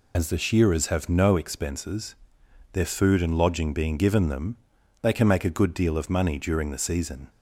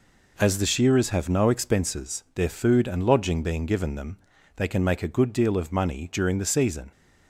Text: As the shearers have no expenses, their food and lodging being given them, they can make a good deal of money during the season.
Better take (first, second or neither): second